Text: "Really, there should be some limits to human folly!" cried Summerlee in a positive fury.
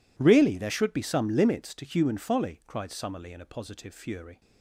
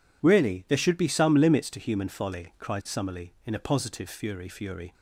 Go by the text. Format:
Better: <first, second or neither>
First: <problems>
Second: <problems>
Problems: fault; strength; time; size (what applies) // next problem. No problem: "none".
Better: first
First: none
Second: says "fury" twice; at 4.4 s